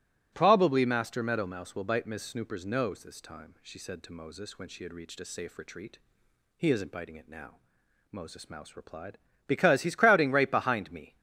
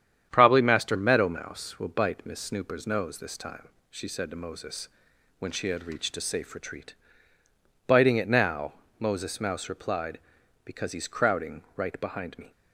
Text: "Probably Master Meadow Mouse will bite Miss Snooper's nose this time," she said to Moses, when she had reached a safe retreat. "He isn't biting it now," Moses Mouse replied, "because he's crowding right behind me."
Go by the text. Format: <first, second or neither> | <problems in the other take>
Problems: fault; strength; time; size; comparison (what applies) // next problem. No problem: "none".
first | starts louder than the rest; strong; until 1.3 s; 9 dB; strong in the first // skips "He isn't"; at 7.4 s